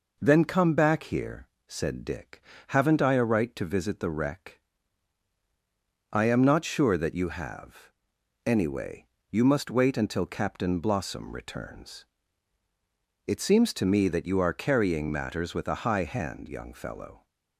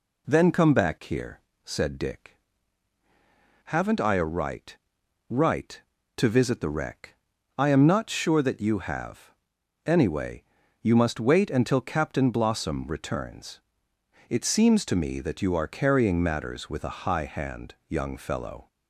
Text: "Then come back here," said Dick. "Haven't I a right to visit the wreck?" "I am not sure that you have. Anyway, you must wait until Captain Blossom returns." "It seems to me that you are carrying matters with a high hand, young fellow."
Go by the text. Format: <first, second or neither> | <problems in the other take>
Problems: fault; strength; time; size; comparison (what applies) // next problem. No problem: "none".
first | says "right" twice; at 5.2 s